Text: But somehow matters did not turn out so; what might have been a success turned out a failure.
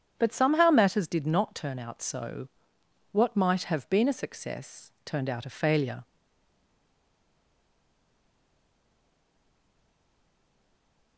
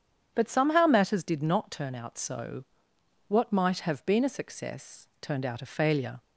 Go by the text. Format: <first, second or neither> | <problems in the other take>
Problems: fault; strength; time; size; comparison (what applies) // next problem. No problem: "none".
second | starts louder than the rest; strong; until 1.1 s; 8.5 dB; strong in the second // stays silent after the last word; strong; from 6.0 s on; 5.1 s long